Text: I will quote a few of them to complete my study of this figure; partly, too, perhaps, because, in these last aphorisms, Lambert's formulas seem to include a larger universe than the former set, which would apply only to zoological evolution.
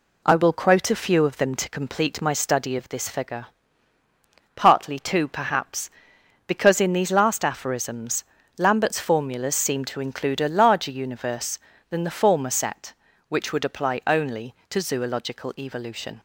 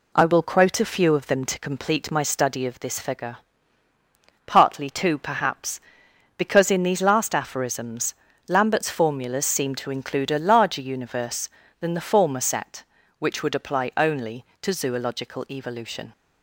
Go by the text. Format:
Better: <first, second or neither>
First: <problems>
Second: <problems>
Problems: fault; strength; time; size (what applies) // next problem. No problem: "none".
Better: neither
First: none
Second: none